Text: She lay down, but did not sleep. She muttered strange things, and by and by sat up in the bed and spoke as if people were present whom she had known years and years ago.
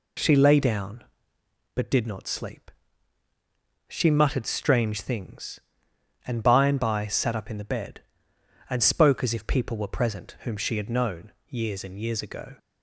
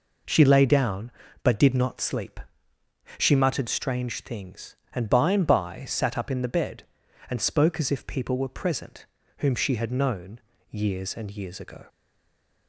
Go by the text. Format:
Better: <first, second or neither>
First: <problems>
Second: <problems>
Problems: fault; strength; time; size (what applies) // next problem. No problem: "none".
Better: first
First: pauses between "known" and "years"; slight; at 11.2 s; 0.16 s long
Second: pauses between "present" and "whom"; slight; at 9.0 s; 0.32 s long // pauses between "known" and "years"; slight; at 10.3 s; 0.30 s long // stays silent after the last word; slight; from 11.8 s on; 0.8 s long